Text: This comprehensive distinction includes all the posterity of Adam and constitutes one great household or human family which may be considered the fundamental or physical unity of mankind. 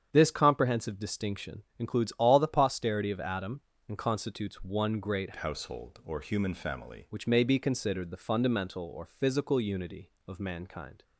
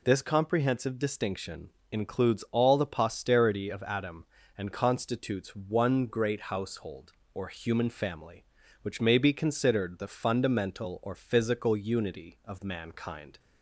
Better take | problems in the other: second | starts louder than the rest; strong; until 1.1 s; 8 dB // pauses between "distinction" and "includes"; slight; at 1.6 s; 0.16 s long; slight in the second // changes voice from "household" to "family"; from 5.3 to 7.0 s; 1.7 s long

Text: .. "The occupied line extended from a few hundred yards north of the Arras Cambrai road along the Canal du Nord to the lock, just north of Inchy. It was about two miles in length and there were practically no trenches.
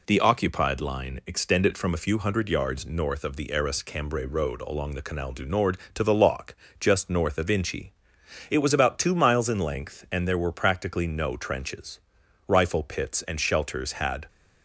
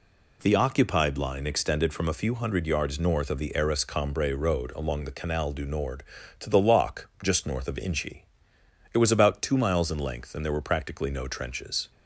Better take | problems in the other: second | goes on to say "Rifle pits and shelters had"; strong; from 12.4 s on; 1.8 s long

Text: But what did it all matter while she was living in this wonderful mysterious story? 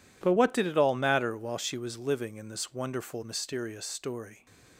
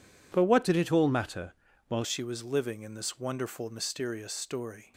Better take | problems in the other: first | changes voice from "did" to "while"; from 0.6 to 2.0 s; 1.4 s long // pauses between "matter" and "while"; slight; at 1.5 s; 0.34 s long

